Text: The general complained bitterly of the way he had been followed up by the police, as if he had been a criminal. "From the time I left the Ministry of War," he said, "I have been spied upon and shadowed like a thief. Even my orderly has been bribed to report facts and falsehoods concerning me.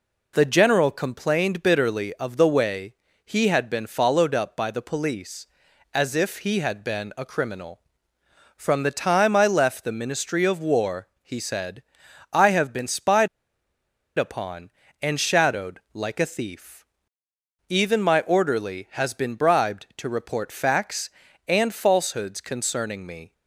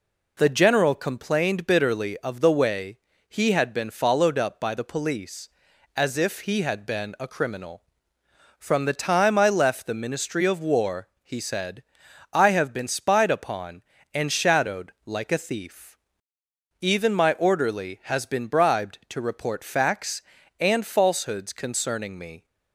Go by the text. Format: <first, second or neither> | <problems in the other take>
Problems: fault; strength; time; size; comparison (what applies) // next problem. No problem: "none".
second | pauses between "way" and "he"; slight; at 2.9 s; 0.30 s long; slight in the second // pauses between "spied" and "upon"; noticeable; at 13.2 s; 0.90 s long